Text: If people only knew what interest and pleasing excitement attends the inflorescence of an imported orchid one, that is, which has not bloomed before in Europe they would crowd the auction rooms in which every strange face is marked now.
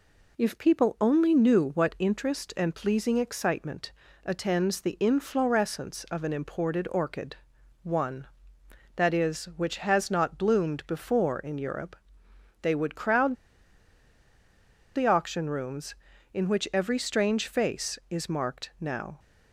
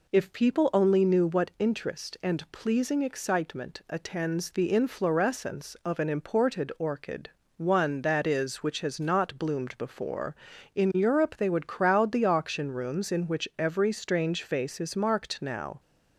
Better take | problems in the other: second | pauses between "excitement" and "attends"; slight; at 3.9 s; 0.34 s long // pauses between "orchid" and "one"; noticeable; at 7.3 s; 0.48 s long; slight in the second // pauses between "Europe" and "they"; noticeable; at 11.9 s; 0.68 s long // pauses between "crowd" and "the"; strong; at 13.3 s; 1.6 s long

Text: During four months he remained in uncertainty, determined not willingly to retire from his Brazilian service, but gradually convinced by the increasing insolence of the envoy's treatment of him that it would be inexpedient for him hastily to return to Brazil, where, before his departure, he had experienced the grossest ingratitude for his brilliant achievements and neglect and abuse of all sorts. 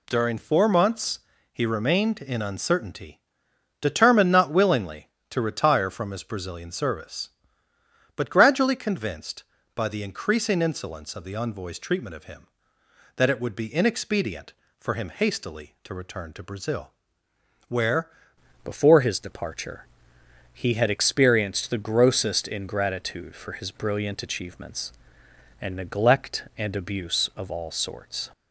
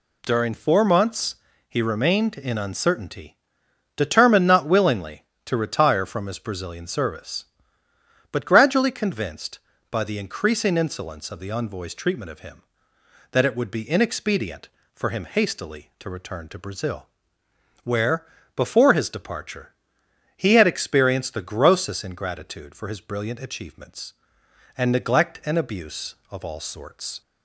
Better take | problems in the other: second | pauses between "months" and "he"; slight; at 1.1 s; 0.32 s long; slight in the second // changes voice at "before"; from 18.6 s on; 9.6 s long

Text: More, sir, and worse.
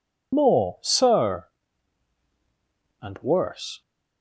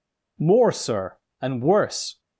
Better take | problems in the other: second | loses the start of "More"; at 0.3 s; 55 ms

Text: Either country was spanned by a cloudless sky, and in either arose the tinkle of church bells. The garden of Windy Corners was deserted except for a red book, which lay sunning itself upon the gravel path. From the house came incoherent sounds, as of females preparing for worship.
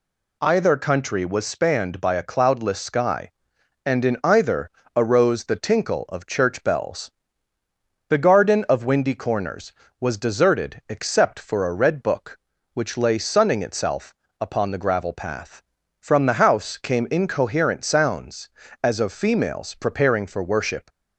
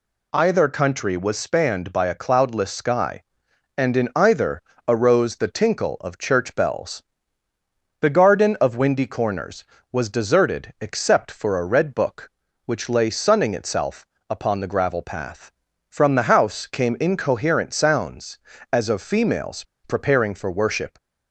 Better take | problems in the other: first | pauses between "either" and "arose"; slight; at 4.6 s; 0.24 s long; slight in the first // pauses between "itself" and "upon"; slight; at 14.0 s; 0.22 s long; slight in the first // pauses between "females" and "preparing"; slight; at 19.6 s; 0.20 s long

